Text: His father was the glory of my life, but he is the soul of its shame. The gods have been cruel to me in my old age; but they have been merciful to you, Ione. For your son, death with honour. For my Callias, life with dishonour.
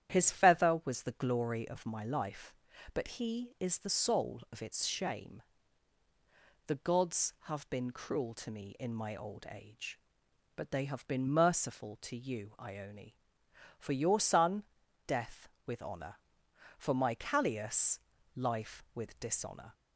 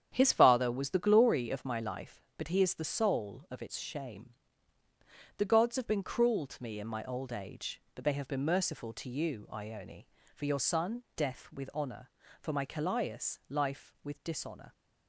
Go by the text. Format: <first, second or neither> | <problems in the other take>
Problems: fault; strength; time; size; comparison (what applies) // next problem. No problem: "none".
second | starts louder than the rest; strong; until 1.1 s; 10 dB; strong in the second // says "feather" for "father"; at 0.2 s